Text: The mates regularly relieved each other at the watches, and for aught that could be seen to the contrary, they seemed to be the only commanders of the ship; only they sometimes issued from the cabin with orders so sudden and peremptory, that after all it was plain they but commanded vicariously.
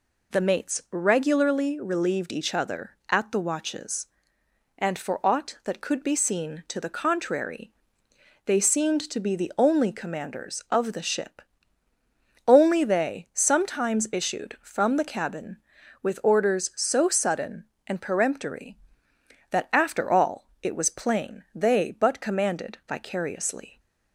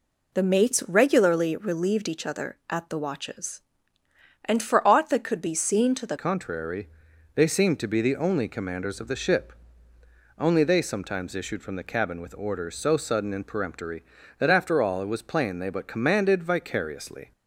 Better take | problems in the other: first | changes voice at "contrary"; from 6.1 s on; 11.2 s long

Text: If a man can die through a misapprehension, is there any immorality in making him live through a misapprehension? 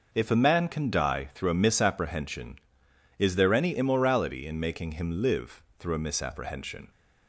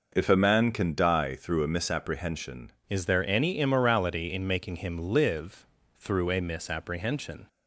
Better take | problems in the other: first | changes voice at "is"; from 2.8 s on; 4.6 s long // pauses between "live" and "through"; slight; at 5.6 s; 0.30 s long; slight in the first

